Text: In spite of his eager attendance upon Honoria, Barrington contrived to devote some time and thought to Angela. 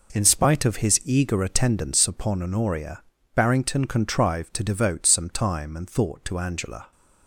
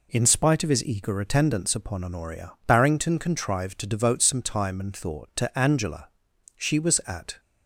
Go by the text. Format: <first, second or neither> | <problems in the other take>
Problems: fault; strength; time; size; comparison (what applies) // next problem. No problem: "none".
first | goes on to say "She was at"; noticeable; from 6.5 s on; 0.84 s long